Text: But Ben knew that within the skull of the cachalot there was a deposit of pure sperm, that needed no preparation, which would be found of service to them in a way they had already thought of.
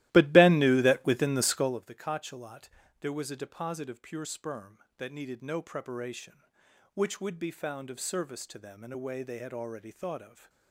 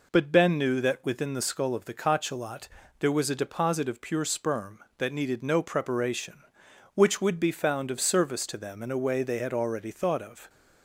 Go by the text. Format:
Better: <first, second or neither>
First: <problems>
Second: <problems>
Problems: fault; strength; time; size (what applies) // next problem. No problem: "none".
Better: second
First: starts louder than the rest; strong; until 1.8 s; 16 dB // pauses between "cachalot" and "there"; slight; at 2.6 s; 0.32 s long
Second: pauses between "cachalot" and "there"; slight; at 2.6 s; 0.32 s long